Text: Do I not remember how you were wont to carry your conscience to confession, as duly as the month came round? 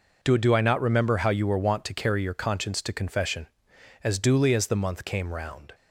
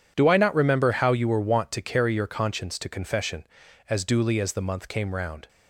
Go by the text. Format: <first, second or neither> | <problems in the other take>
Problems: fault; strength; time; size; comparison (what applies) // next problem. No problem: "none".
second | says "Do" twice; at 0.3 s